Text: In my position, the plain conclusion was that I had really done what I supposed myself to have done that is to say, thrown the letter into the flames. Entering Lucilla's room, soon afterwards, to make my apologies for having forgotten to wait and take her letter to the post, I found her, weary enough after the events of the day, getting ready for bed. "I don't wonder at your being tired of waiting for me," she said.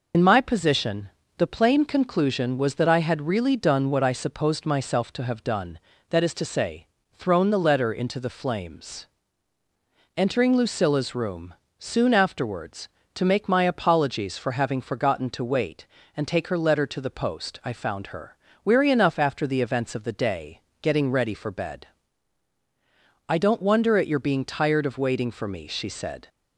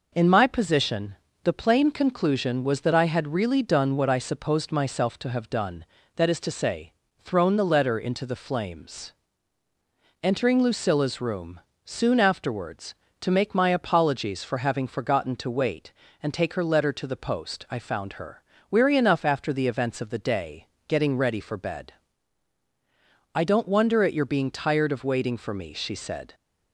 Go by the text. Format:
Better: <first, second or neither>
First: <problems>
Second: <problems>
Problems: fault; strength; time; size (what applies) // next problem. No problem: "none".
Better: second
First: loses the start of "In"; at 0.1 s; 65 ms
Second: none